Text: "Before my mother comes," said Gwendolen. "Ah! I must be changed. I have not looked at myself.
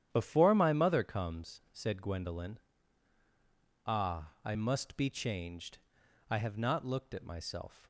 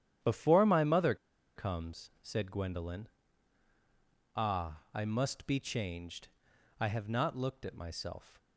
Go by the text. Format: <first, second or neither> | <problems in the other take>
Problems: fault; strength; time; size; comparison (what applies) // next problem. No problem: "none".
first | starts louder than the rest; strong; until 1.6 s; 10 dB; strong in the first // pauses between "mother" and "comes"; at 1.1 s; 0.40 s long